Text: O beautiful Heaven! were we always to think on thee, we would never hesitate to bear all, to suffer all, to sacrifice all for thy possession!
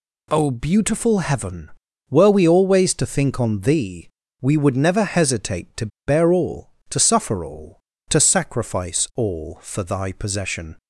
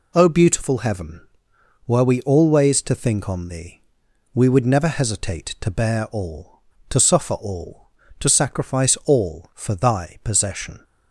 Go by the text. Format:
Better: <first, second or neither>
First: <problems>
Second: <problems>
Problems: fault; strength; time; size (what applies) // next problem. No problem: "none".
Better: second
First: pauses between "to" and "bear"; slight; at 5.8 s; 0.19 s long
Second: none